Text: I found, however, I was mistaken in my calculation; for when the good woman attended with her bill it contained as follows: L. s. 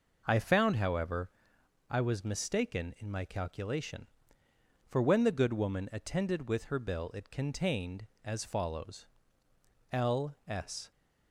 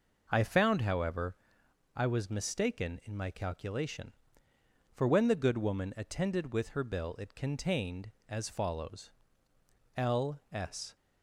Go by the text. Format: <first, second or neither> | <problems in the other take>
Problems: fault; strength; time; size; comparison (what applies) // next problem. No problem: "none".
neither | none